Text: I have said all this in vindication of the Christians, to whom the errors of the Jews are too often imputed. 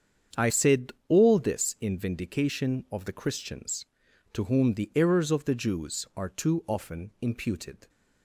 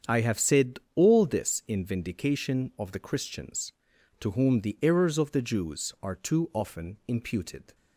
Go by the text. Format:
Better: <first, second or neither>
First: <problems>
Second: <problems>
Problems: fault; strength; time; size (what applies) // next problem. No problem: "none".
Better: second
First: starts louder than the rest; strong; until 1.5 s; 7.5 dB // skips "have"; at 0.5 s // pauses between "said" and "all"; slight; at 0.9 s; 0.16 s long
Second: starts louder than the rest; strong; until 1.2 s; 8 dB // pauses between "said" and "all"; slight; at 0.7 s; 0.16 s long